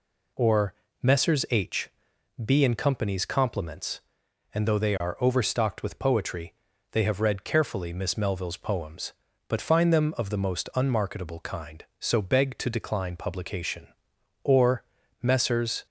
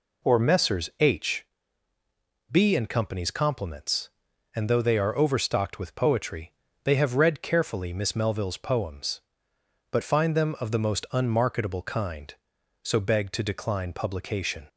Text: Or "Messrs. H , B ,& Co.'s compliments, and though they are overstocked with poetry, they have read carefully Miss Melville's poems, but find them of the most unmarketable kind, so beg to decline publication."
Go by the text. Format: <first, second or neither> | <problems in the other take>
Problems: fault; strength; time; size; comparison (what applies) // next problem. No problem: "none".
second | pauses between "Or" and "Messrs"; slight; at 0.7 s; 0.28 s long // goes on to say "Or Messrs"; from 14.4 s on; 1.4 s long